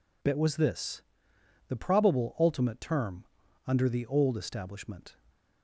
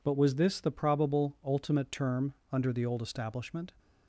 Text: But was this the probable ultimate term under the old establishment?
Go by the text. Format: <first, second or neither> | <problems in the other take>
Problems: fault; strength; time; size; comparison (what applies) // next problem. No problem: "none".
second | says "Bit" for "But"; at 0.2 s // pauses between "this" and "the"; noticeable; at 1.0 s; 0.66 s long // pauses between "term" and "under"; at 3.2 s; 0.42 s long; slight in the second